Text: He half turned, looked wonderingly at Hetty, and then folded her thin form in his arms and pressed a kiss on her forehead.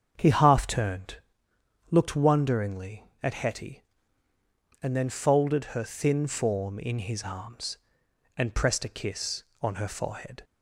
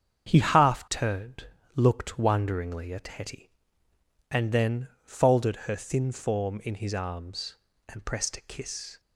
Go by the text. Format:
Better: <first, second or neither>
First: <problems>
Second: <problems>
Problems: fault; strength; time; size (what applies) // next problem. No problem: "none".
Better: first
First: starts louder than the rest; strong; until 1.1 s; 7 dB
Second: starts louder than the rest; strong; until 1.3 s; 8 dB // pauses between "then" and "folded"; slight; at 4.8 s; 0.18 s long // stops before "on her forehead"; at 8.9 s